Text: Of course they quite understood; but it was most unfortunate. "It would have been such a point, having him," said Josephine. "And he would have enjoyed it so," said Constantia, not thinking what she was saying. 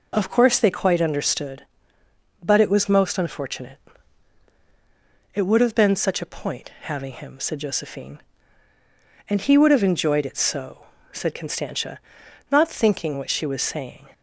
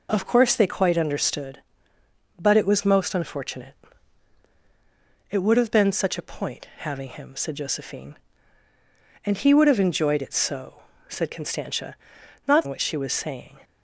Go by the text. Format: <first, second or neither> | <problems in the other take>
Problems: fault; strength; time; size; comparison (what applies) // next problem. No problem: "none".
first | skips "thinking"; at 12.6 s